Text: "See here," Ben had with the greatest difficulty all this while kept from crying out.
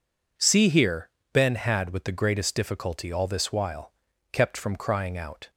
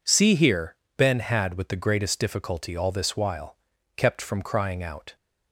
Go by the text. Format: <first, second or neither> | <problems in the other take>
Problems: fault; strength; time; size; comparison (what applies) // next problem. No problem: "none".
neither | pauses between "while" and "kept"; the same in both